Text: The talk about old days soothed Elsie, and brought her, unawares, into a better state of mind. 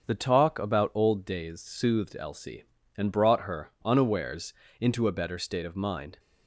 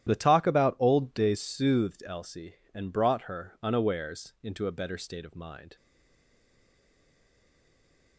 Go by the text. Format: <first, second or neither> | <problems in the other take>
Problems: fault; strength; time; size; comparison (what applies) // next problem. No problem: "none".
first | starts louder than the rest; strong; until 1.1 s; 11.5 dB; also in the first // stays silent after the last word; from 5.7 s on; 2.4 s long